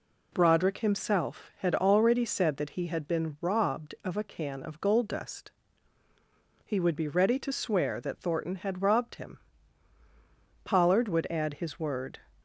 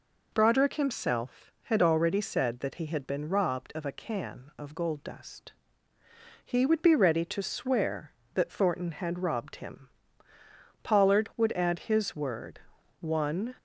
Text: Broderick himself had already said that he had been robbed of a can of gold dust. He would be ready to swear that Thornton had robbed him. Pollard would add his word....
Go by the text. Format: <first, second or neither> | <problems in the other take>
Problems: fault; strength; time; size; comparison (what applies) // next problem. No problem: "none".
first | goes on to say "One"; from 12.9 s on; 0.56 s long